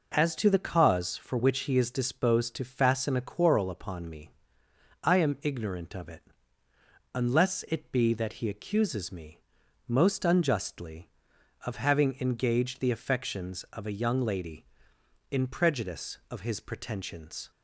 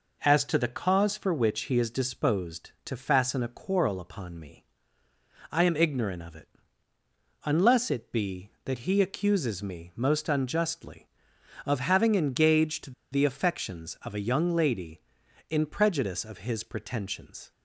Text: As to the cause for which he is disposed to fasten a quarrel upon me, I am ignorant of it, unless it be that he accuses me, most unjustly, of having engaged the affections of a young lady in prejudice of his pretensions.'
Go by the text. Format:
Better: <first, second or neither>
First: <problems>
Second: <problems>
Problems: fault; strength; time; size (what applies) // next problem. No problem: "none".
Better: first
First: none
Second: pauses between "engaged" and "the"; slight; at 12.9 s; 0.18 s long